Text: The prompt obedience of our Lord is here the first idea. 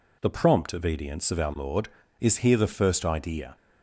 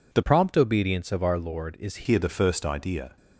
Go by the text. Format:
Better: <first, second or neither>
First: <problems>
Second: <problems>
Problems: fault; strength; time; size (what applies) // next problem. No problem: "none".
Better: first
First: none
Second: changes voice from "prompt" to "is"; from 0.2 to 2.0 s; 1.8 s long